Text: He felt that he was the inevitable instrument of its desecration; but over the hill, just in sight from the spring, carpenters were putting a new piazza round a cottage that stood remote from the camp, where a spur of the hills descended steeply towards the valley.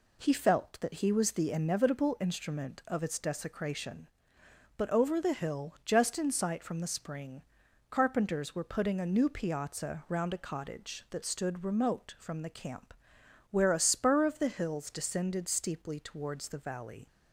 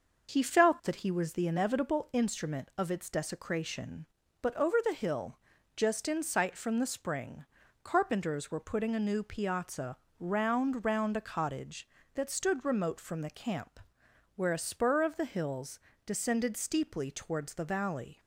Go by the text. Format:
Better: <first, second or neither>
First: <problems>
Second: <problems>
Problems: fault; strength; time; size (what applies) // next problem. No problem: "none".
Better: first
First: none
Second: pauses between "piazza" and "round"; slight; at 9.9 s; 0.22 s long // says "round" twice; at 10.8 s // pauses between "hills" and "descended"; slight; at 15.7 s; 0.26 s long